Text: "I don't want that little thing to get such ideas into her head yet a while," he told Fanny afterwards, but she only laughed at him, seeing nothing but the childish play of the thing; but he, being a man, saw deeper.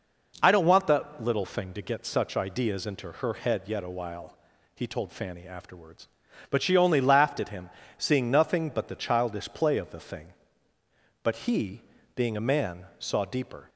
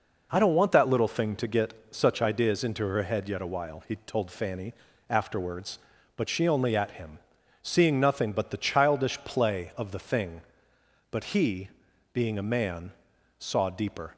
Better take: first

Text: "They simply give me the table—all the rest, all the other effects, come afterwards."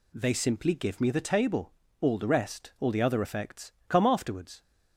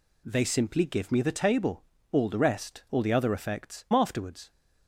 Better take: first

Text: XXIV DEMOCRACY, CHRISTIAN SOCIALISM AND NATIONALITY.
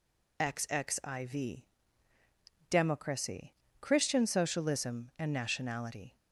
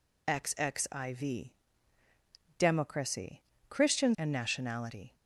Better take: first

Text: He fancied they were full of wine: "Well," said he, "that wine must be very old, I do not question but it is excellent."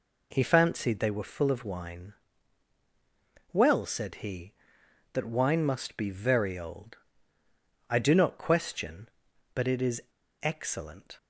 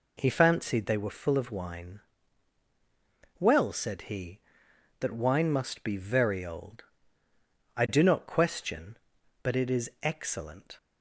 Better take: second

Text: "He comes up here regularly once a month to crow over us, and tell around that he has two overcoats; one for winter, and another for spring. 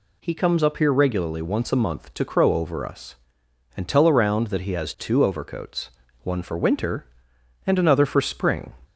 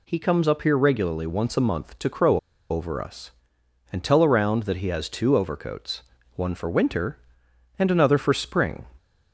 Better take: first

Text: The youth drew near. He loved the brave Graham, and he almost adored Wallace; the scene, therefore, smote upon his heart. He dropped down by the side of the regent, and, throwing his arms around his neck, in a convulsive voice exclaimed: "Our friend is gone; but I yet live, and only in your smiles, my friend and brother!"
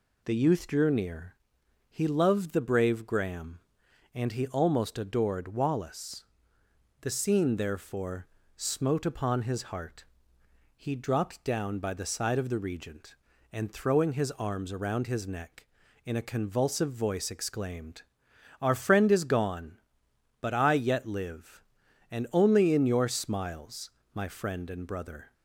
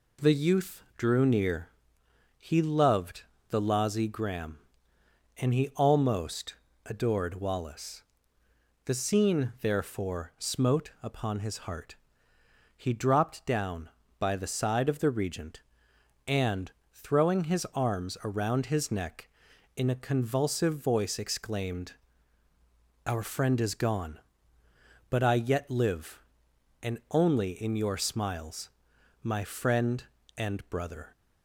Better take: first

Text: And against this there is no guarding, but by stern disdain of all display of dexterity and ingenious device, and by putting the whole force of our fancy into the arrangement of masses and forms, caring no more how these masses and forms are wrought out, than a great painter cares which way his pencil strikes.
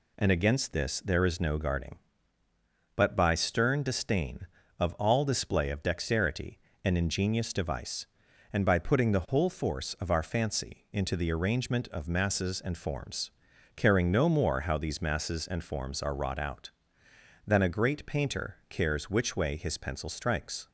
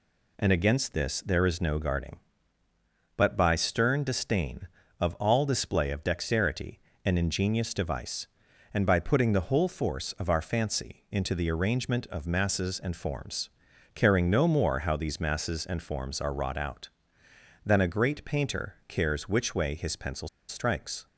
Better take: first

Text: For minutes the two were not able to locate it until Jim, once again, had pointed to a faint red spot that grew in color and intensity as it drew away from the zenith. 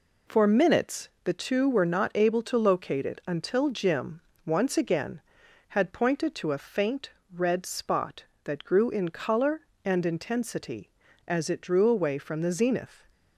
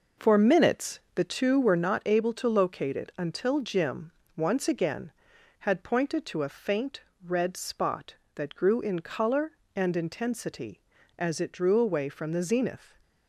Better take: first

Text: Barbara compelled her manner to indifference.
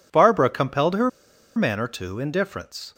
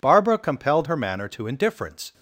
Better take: second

